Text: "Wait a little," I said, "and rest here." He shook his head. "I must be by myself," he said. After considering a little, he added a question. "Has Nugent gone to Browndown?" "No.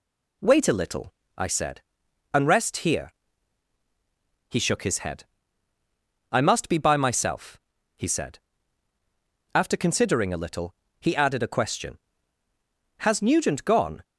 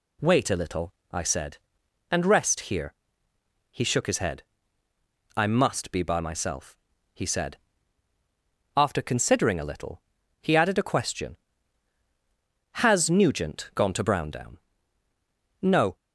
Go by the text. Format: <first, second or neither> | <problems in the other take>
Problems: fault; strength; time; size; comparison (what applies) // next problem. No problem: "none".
second | stops before "to Browndown No"; at 14.0 s